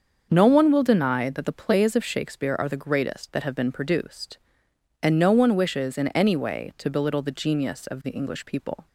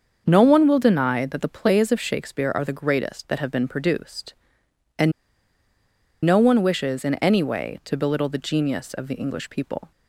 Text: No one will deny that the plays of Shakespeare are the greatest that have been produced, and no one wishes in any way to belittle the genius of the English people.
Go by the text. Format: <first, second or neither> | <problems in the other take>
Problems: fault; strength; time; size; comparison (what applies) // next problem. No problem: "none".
first | starts louder than the rest; until 1.2 s; 6.5 dB; also in the first // pauses between "and" and "no"; at 5.1 s; 1.1 s long